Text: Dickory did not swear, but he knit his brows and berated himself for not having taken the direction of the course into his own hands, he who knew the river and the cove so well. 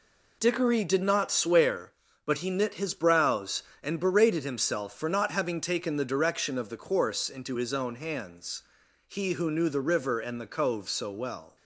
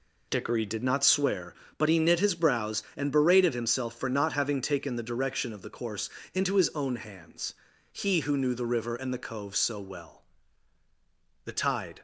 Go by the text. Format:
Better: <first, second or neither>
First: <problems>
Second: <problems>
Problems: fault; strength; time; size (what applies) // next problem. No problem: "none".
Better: first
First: none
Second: pauses between "course" and "into"; slight; at 6.0 s; 0.26 s long // goes on to say "The tide"; from 11.4 s on; 0.56 s long